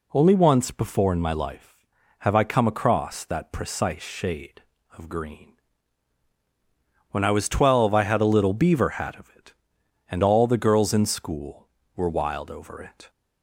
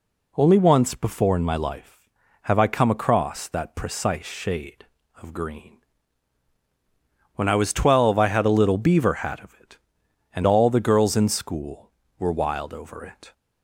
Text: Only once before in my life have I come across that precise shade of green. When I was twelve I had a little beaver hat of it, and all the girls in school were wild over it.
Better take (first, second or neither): neither